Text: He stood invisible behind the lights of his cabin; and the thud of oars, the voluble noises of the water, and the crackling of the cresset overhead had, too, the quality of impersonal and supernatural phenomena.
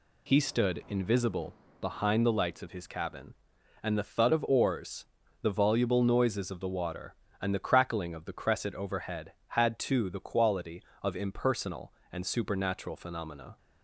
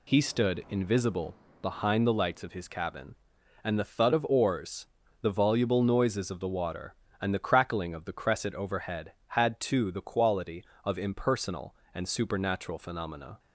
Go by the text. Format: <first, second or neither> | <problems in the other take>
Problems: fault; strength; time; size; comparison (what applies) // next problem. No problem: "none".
neither | pauses between "invisible" and "behind"; slight; the same in both